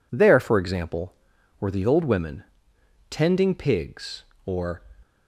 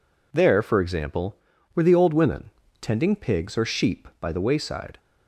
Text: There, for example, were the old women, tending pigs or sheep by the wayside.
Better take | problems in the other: second | stops before "sheep by the wayside"; at 5.0 s

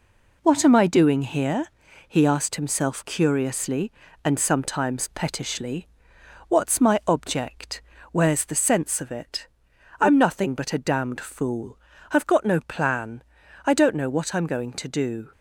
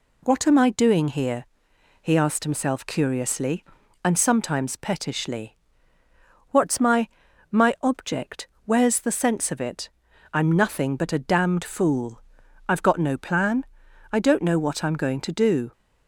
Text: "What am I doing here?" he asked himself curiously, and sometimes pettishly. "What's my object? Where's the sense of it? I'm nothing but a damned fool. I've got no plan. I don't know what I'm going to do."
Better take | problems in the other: first | says "my" twice; at 7.5 s

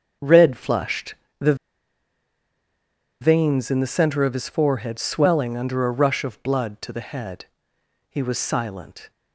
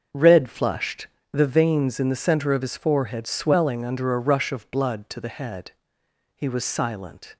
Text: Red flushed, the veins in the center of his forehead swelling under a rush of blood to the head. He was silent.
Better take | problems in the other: second | starts louder than the rest; until 1.4 s; 6.5 dB; also in the second // pauses between "the" and "veins"; strong; at 1.5 s; 1.6 s long

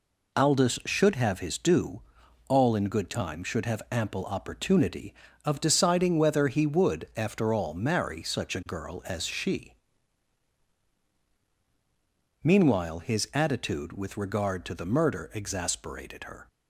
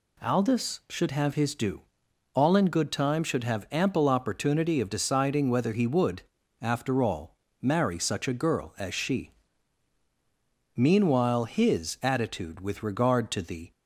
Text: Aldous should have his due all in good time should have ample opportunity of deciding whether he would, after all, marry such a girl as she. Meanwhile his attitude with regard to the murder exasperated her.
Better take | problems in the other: first | pauses between "due" and "all"; noticeable; at 1.8 s; 0.52 s long; noticeable in the first // stops before "murder exasperated her"; at 13.7 s

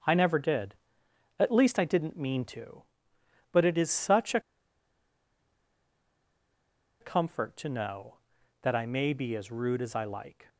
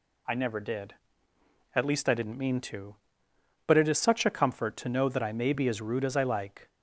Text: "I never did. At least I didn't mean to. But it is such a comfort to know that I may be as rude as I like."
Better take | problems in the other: second | starts louder than the rest; until 1.7 s; 7 dB // pauses between "a" and "comfort"; strong; at 4.3 s; 2.6 s long

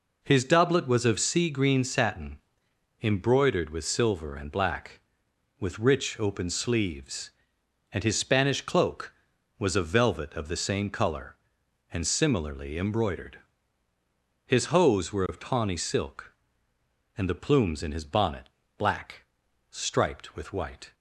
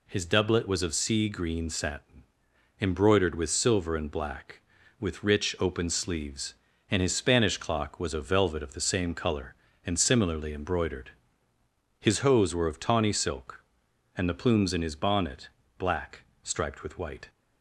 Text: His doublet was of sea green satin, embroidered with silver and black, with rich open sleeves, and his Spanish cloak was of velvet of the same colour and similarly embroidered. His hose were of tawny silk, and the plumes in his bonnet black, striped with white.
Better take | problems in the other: first | says "clock" for "cloak"; at 7.5 s // pauses between "bonnet" and "black"; slight; at 15.4 s; 0.28 s long; slight in the first

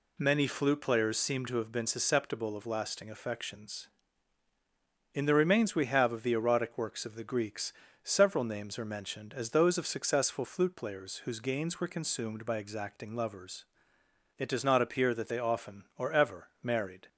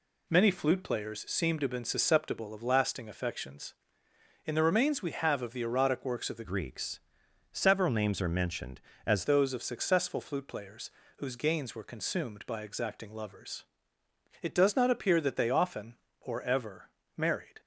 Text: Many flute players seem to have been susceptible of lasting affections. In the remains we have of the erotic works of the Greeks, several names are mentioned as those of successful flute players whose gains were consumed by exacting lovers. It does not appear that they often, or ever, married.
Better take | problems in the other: first | changes voice from "Greeks" to "as"; from 6.4 to 9.2 s; 2.8 s long // pauses between "players" and "whose"; slight; at 10.9 s; 0.28 s long

